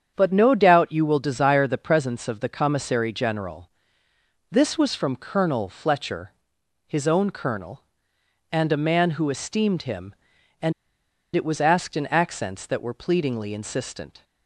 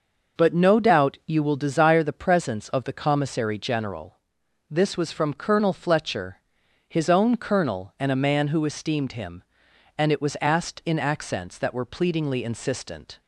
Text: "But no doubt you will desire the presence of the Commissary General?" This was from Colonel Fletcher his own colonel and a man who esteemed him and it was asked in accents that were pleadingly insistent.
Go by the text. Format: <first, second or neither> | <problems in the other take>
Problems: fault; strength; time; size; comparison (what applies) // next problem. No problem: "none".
second | starts louder than the rest; strong; until 1.1 s; 8 dB // pauses between "Fletcher" and "his"; noticeable; at 6.3 s; 0.56 s long; noticeable in the second // pauses between "and" and "it"; noticeable; at 10.7 s; 0.63 s long